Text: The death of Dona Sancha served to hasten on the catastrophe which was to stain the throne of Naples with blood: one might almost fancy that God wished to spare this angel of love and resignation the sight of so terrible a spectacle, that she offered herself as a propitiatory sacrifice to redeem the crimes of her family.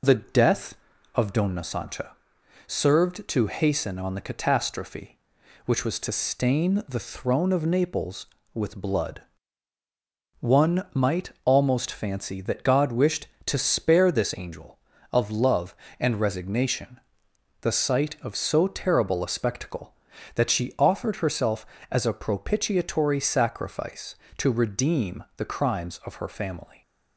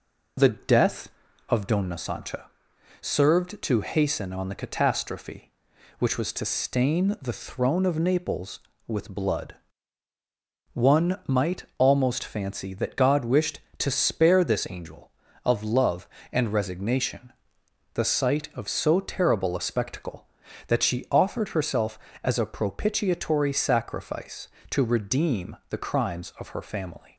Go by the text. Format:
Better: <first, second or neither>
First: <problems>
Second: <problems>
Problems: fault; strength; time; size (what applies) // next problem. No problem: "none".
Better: neither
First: pauses between "Sancha" and "served"; noticeable; at 2.1 s; 0.56 s long // pauses between "might" and "almost"; slight; at 11.3 s; 0.16 s long // pauses between "resignation" and "the"; noticeable; at 17.0 s; 0.62 s long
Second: pauses between "Sancha" and "served"; noticeable; at 2.4 s; 0.56 s long // pauses between "might" and "almost"; slight; at 11.6 s; 0.16 s long // pauses between "resignation" and "the"; noticeable; at 17.3 s; 0.62 s long